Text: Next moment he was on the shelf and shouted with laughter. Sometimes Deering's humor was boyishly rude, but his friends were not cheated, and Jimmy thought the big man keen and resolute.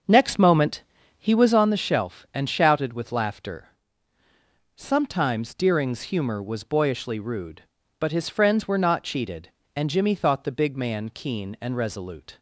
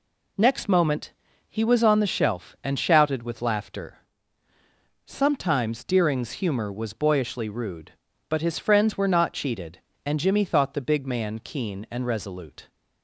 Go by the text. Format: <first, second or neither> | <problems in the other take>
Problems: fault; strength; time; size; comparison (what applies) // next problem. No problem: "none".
second | starts louder than the rest; until 1.7 s; 6.5 dB // pauses between "moment" and "he"; slight; at 0.8 s; 0.36 s long; slight in the second